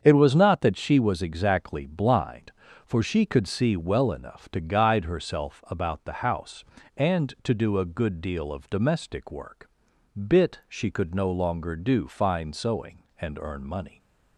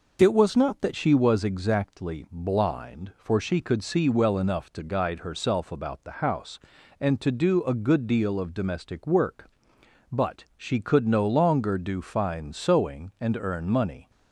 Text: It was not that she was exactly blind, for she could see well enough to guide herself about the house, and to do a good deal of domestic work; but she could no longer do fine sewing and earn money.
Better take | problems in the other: second | starts louder than the rest; strong; until 1.0 s; 7.5 dB // says "bit" for "but"; at 10.2 s

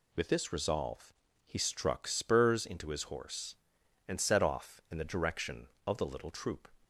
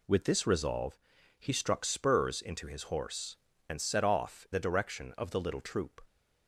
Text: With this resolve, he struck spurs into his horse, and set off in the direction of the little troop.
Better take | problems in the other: first | skips "in"; at 4.4 s

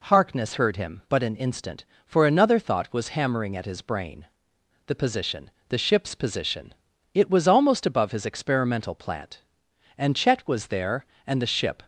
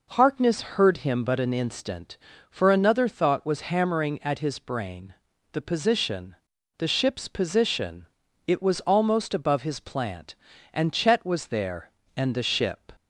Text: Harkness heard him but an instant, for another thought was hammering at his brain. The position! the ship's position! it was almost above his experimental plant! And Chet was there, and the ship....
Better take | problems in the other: first | skips "experimental"; at 9.7 s

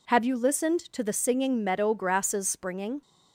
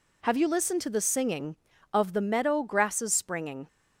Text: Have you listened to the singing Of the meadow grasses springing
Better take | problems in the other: second | skips "Of the"; at 1.6 s

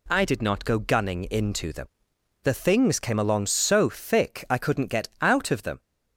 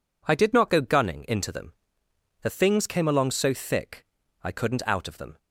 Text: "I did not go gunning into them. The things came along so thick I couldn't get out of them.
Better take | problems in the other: first | pauses between "thick" and "I"; at 4.0 s; 0.38 s long // skips "get"; at 4.8 s

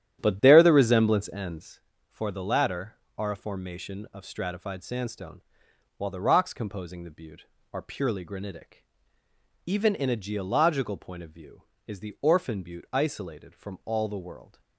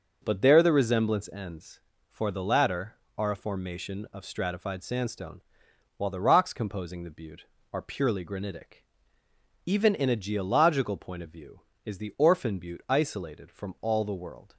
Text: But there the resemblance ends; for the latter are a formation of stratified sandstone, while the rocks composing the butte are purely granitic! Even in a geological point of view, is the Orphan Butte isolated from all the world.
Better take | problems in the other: second | starts louder than the rest; strong; until 1.8 s; 10.5 dB

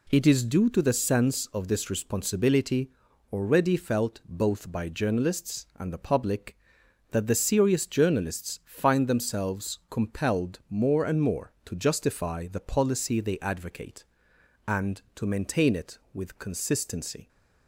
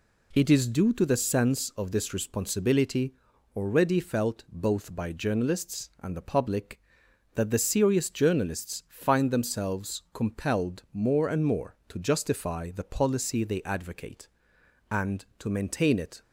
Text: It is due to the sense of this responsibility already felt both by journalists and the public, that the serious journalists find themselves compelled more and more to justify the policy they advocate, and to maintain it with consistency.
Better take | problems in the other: first | pauses between "responsibility" and "already"; at 3.1 s; 0.40 s long; also in the first // stops before "with consistency"; at 16.2 s

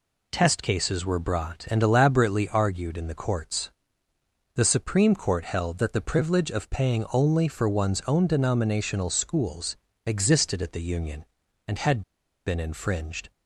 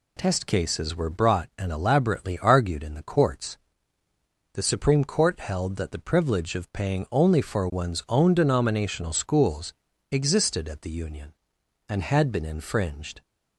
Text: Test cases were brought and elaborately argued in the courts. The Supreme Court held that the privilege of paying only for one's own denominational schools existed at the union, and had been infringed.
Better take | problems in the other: second | pauses between "schools" and "existed"; slight; at 9.7 s; 0.30 s long; also in the second // pauses between "had" and "been"; at 12.0 s; 0.44 s long

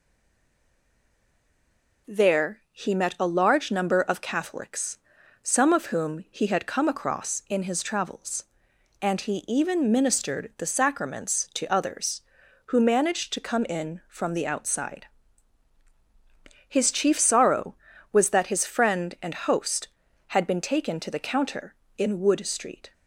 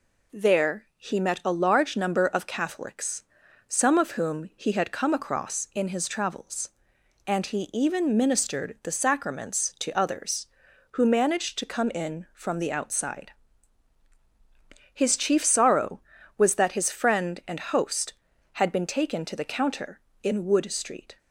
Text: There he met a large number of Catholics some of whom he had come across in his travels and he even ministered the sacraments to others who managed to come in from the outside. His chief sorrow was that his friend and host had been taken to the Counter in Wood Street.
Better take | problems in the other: second | stays silent before the first word; noticeable; until 2.0 s; 2.0 s long // pauses between "Catholics" and "some"; noticeable; at 4.9 s; 0.46 s long; noticeable in the second

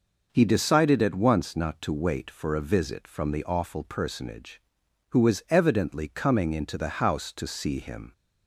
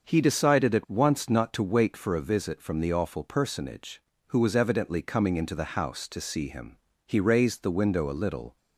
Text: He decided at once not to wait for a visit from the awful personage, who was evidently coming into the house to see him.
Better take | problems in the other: first | starts louder than the rest; until 1.1 s; 6.5 dB // goes on to say "He raised the window a little"; from 7.0 s on; 1.5 s long

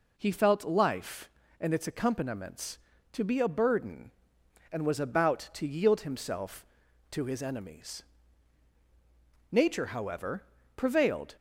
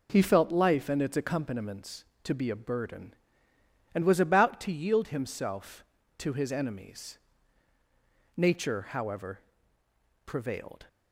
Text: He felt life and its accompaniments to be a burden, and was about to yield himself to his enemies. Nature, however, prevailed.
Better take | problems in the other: neither | none

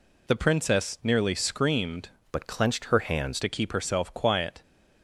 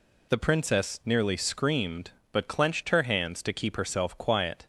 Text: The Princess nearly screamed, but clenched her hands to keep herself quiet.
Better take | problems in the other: second | changes voice from "but" to "hands"; from 2.3 to 3.4 s; 1.1 s long

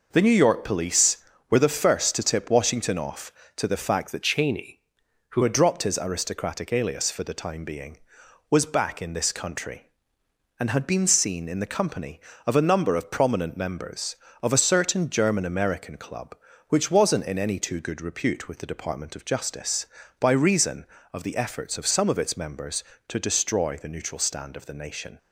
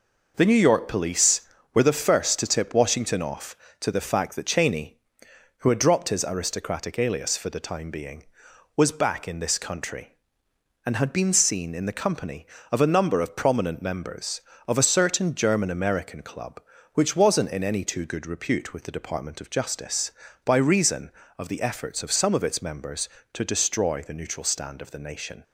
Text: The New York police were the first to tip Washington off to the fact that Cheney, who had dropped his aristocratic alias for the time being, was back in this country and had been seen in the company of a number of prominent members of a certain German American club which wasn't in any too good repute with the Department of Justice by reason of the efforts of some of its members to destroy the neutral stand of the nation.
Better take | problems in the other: second | changes voice from "Cheney" to "who"; from 4.2 to 5.4 s; 1.2 s long

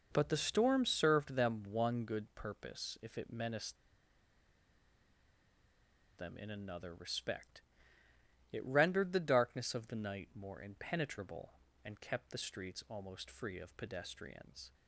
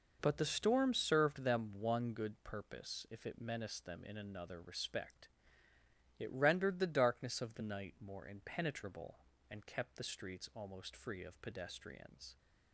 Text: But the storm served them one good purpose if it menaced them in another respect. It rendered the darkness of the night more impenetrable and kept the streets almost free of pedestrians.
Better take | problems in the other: second | pauses between "menaced" and "them"; strong; at 3.7 s; 2.4 s long

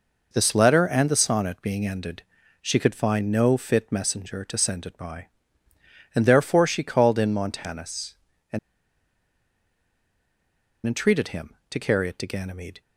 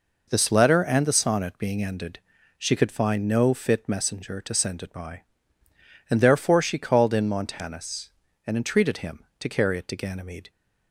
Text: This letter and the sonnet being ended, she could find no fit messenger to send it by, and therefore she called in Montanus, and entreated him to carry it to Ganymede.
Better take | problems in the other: second | pauses between "and" and "entreated"; strong; at 8.5 s; 2.2 s long

